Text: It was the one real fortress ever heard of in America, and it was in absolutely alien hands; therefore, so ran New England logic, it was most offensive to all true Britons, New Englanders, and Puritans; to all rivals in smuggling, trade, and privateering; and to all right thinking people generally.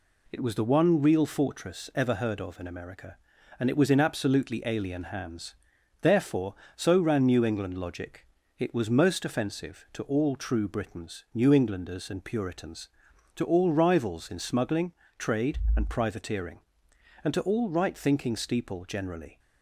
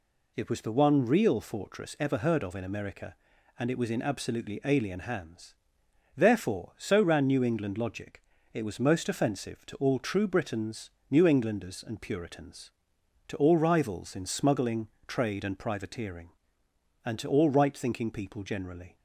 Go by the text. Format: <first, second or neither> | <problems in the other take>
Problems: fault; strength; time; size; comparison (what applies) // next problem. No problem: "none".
second | says "steeple" for "people"; at 18.3 s